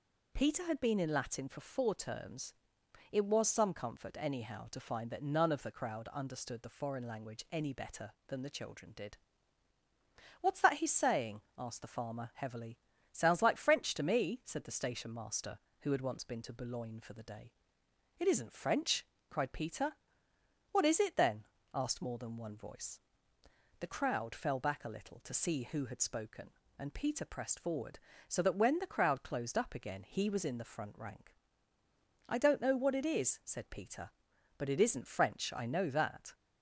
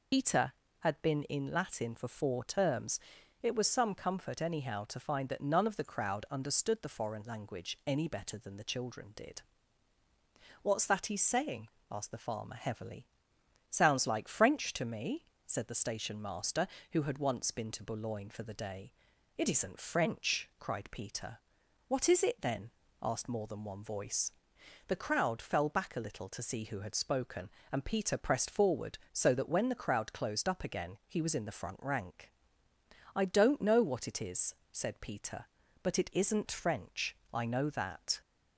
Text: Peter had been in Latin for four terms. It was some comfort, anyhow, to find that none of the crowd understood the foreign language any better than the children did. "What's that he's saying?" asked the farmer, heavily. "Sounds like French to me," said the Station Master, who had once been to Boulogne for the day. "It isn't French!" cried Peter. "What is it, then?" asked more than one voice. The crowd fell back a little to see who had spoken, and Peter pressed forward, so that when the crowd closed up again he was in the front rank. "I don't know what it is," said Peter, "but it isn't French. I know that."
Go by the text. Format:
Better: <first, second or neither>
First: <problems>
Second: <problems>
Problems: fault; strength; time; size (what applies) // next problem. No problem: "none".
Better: first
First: none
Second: loses the start of "Peter"; at 0.1 s; 60 ms